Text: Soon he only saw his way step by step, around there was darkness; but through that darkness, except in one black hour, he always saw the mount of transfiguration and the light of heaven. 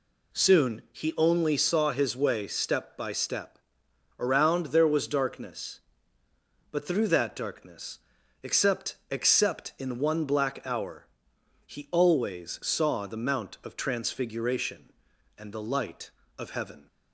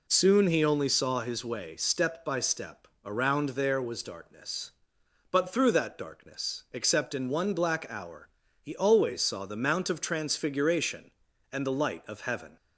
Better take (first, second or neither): second